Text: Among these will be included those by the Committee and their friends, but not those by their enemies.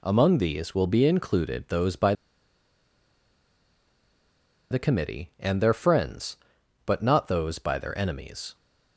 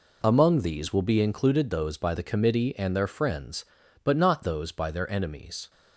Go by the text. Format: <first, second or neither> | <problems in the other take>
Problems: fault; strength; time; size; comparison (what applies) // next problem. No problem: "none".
second | pauses between "by" and "the"; strong; at 2.1 s; 2.5 s long